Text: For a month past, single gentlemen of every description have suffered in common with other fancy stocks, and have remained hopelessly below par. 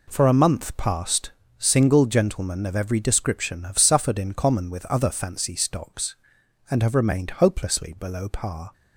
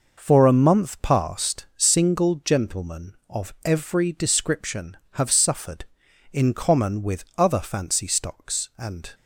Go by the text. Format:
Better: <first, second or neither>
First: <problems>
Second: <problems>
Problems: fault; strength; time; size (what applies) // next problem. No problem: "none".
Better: first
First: none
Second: stops before "have remained hopelessly below par"; at 9.1 s